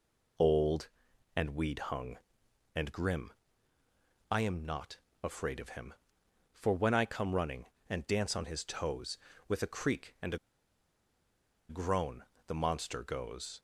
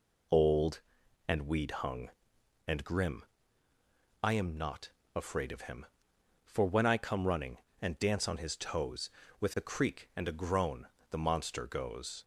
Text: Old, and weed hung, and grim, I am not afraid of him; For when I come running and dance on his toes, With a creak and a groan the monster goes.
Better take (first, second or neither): second